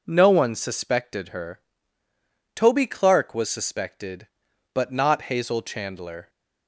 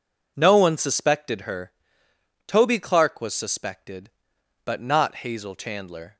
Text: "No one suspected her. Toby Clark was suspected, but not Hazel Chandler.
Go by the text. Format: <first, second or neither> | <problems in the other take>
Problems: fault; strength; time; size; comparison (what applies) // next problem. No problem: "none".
neither | none